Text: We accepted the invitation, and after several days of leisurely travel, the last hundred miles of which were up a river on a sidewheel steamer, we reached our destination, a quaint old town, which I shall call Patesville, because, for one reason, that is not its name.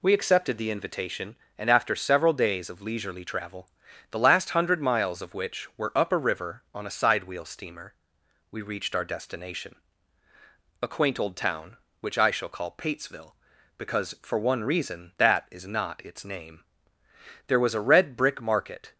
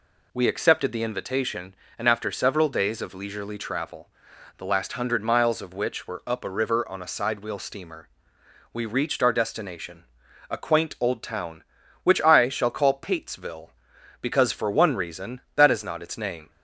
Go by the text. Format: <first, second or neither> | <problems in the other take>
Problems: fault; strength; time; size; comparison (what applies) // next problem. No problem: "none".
second | goes on to say "There was a red brick market"; from 17.4 s on; 1.4 s long